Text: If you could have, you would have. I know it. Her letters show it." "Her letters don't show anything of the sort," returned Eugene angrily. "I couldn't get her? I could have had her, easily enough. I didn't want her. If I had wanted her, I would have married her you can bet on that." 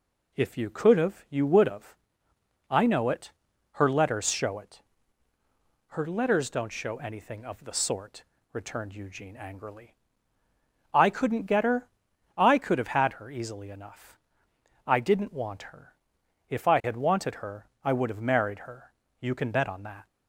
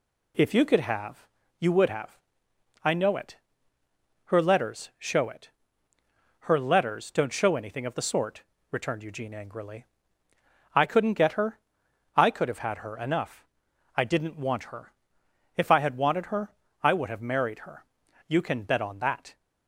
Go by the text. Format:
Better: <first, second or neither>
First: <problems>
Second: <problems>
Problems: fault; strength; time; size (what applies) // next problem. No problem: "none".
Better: first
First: pauses between "her" and "you"; slight; at 18.9 s; 0.30 s long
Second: skips "easily"; at 12.9 s // pauses between "her" and "you"; at 17.8 s; 0.42 s long